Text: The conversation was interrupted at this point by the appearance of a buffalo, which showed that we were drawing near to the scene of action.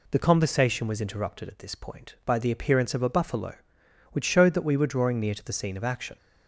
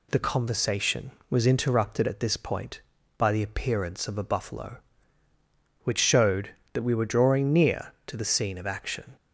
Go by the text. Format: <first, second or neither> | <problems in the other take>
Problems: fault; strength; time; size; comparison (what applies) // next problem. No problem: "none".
neither | none